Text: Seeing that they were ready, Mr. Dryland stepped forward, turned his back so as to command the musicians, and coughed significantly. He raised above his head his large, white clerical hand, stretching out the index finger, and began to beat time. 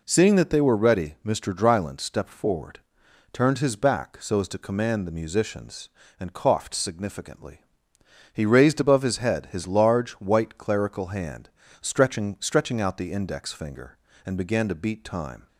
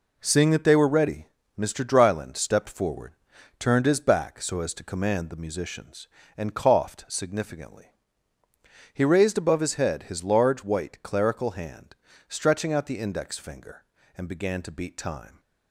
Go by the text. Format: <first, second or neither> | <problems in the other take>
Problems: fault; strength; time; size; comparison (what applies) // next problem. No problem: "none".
second | says "stretching" twice; at 12.3 s